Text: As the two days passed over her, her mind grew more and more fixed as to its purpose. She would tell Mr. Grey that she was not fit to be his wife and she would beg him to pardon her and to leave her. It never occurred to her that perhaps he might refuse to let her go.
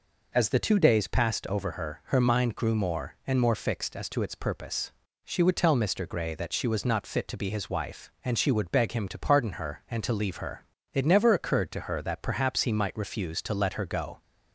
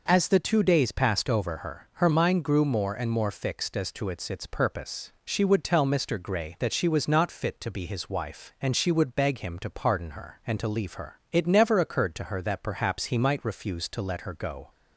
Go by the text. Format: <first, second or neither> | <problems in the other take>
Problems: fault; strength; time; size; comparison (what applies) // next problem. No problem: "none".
first | says "its" twice; at 4.3 s